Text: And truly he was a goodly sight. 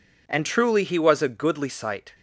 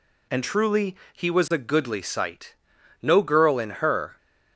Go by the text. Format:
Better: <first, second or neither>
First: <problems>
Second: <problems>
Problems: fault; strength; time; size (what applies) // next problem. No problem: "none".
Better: first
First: none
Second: pauses between "truly" and "he"; slight; at 0.9 s; 0.18 s long // goes on to say "No girl in her"; noticeable; from 3.0 s on; 1.1 s long